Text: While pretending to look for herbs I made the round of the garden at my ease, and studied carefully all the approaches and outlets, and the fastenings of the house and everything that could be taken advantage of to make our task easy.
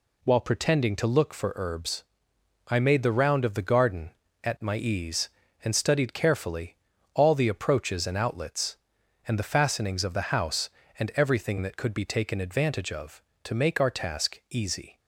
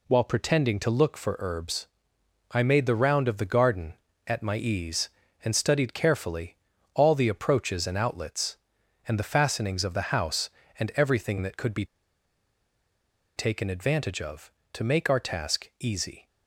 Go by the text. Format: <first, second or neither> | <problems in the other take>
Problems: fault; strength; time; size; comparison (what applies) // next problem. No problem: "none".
first | pauses between "herbs" and "I"; noticeable; at 1.8 s; 0.64 s long; noticeable in the first // pauses between "carefully" and "all"; at 6.5 s; 0.38 s long; also in the first // pauses between "be" and "taken"; strong; at 11.8 s; 1.5 s long